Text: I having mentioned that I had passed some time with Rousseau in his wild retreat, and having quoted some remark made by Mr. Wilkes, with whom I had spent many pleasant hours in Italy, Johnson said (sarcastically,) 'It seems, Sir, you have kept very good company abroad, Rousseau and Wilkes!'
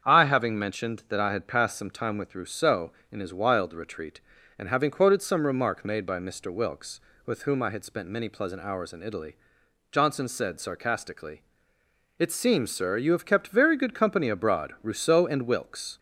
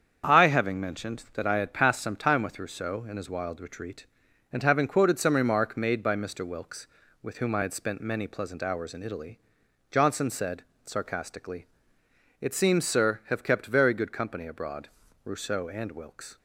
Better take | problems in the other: first | starts louder than the rest; strong; until 1.3 s; 7.5 dB; strong in the first // skips "you"; at 13.2 s

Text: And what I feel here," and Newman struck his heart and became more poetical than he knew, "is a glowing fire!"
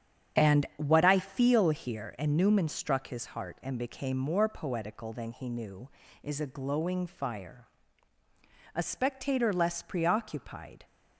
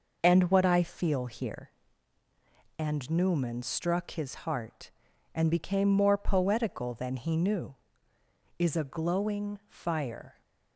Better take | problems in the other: second | starts louder than the rest; strong; until 1.4 s; 8.5 dB // goes on to say "A spectator less preoccupied"; strong; from 8.7 s on; 2.1 s long

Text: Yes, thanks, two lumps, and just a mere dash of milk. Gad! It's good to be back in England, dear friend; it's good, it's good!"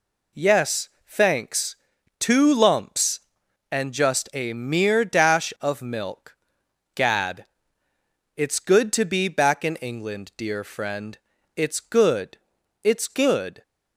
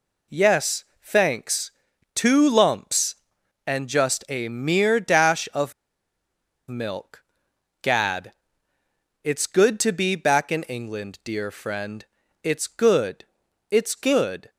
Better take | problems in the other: first | pauses between "of" and "milk"; noticeable; at 5.7 s; 0.95 s long

